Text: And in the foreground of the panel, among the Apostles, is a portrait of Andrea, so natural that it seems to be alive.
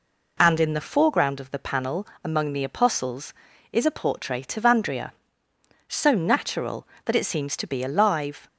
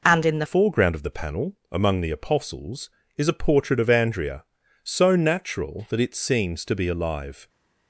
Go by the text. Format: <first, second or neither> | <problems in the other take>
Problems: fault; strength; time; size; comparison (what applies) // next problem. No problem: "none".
first | changes voice at "foreground"; from 0.4 s on; 7.0 s long